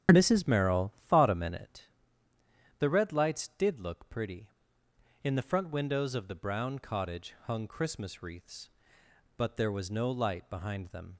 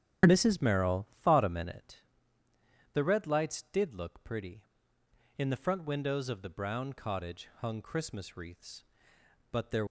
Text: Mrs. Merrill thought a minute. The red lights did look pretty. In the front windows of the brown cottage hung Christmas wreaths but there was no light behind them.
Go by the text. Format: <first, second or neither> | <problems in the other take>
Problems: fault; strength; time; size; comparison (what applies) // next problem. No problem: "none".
first | starts louder than the rest; strong; until 1.4 s; 10 dB; strong in the first // stops before "was no light behind them"; at 9.8 s